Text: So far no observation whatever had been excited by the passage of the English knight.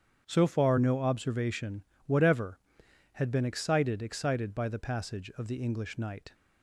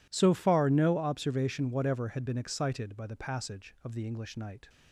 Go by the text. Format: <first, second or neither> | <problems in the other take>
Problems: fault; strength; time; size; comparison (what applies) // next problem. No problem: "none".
second | starts louder than the rest; strong; until 1.2 s; 8 dB // pauses between "observation" and "whatever"; slight; at 1.8 s; 0.22 s long // says "excited" twice; at 4.0 s